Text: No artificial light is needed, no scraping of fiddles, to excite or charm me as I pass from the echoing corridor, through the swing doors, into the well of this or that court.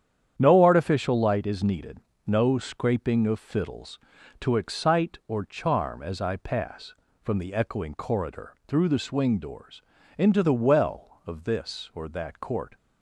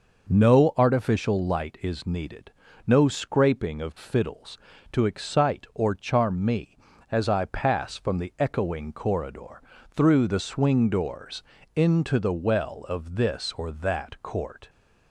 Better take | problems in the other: second | starts louder than the rest; strong; until 1.3 s; 9 dB // skips "me"; at 6.0 s

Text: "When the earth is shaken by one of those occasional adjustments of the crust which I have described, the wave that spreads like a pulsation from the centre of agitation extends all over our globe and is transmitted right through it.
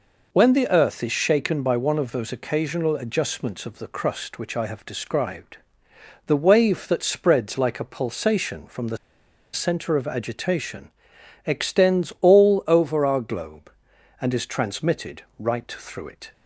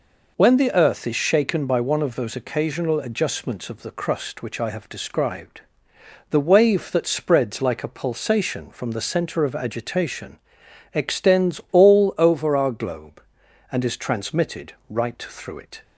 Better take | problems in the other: second | pauses between "the" and "centre"; noticeable; at 8.9 s; 0.58 s long // pauses between "agitation" and "extends"; noticeable; at 10.9 s; 0.56 s long; noticeable in the second // pauses between "transmitted" and "right"; slight; at 15.2 s; 0.16 s long; slight in the second

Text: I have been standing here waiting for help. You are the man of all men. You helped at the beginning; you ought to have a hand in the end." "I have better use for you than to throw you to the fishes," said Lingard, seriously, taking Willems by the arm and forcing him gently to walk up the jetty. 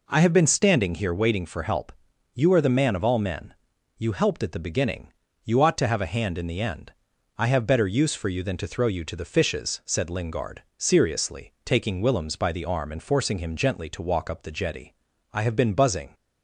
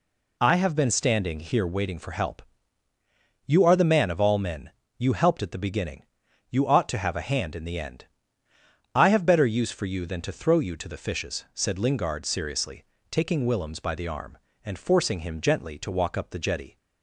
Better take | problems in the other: second | goes on to say "I have been buzzing"; noticeable; from 15.3 s on; 0.82 s long

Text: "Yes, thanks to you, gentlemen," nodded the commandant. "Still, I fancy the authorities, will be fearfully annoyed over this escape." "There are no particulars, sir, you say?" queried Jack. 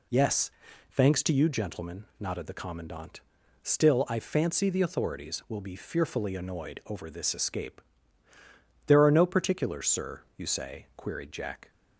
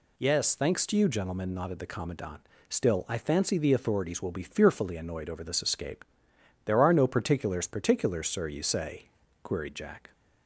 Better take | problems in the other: first | says "particulars" twice; at 7.6 s

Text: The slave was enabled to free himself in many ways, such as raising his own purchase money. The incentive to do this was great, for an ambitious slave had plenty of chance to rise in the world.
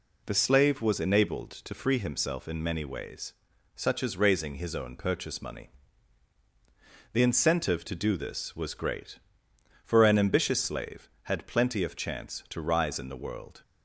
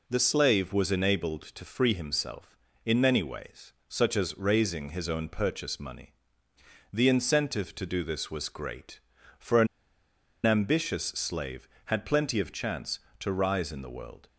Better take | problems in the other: first | pauses between "an" and "ambitious"; noticeable; at 9.6 s; 0.79 s long

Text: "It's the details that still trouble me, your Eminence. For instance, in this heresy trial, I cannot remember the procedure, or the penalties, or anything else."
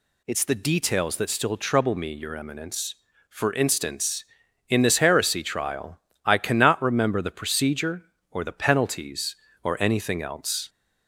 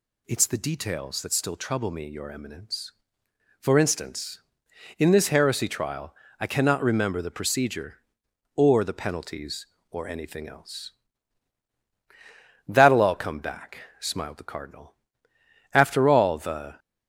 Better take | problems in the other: first | goes on to say "That'll all come back smiled the Cardinal After all the"; strong; from 12.6 s on; 4.1 s long

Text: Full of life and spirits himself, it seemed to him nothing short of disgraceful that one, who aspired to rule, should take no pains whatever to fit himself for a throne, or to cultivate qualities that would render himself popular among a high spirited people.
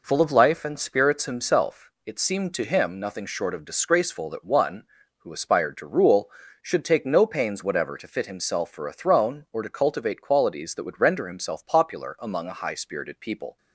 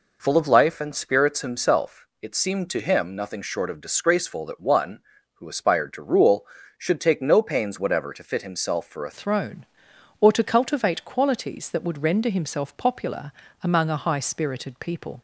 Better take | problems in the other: first | changes voice at "throne"; from 9.1 s on; 6.1 s long // pauses between "popular" and "among"; slight; at 13.3 s; 0.30 s long

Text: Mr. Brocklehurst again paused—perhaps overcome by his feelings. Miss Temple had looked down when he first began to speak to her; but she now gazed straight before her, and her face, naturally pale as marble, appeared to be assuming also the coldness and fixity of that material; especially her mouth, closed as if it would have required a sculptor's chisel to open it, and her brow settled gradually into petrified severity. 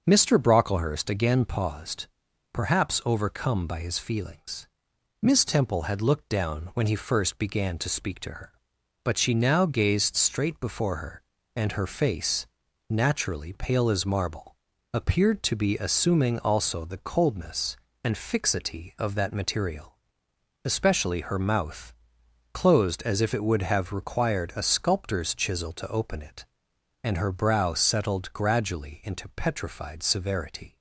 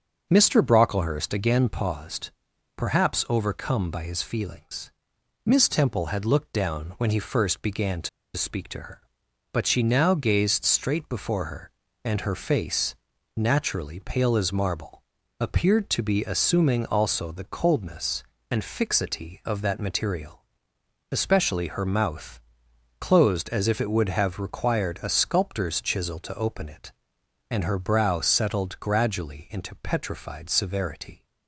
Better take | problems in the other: first | starts louder than the rest; until 1.3 s; 6.5 dB; also in the first // pauses between "to" and "speak"; slight; at 8.0 s; 0.27 s long

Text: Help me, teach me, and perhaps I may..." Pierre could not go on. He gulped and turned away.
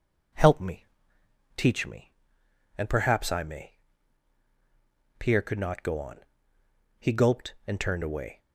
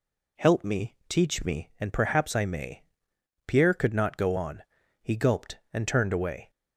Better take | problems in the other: neither | none

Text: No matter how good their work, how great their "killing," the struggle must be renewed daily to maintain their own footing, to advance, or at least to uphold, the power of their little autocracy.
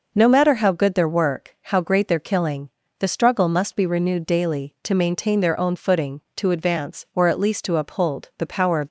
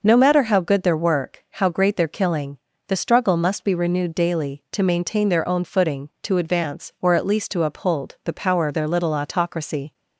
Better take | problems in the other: second | stops before "their little autocracy"; at 8.8 s

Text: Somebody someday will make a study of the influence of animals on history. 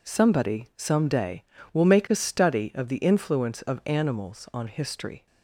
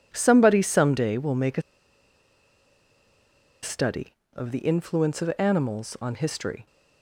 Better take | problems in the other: first | pauses between "a" and "study"; strong; at 1.6 s; 2.0 s long

